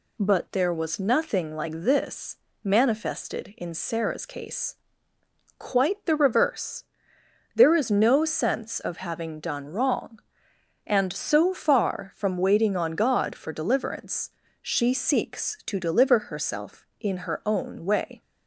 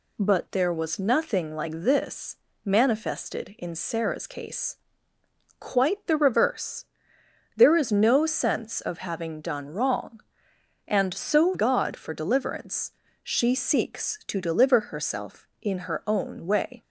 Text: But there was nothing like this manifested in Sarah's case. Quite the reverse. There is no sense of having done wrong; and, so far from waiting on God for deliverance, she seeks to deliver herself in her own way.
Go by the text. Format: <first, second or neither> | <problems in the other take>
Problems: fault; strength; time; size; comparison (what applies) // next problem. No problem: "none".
first | pauses between "this" and "manifested"; slight; at 2.3 s; 0.28 s long; slight in the first // skips "far from waiting on"; at 11.5 s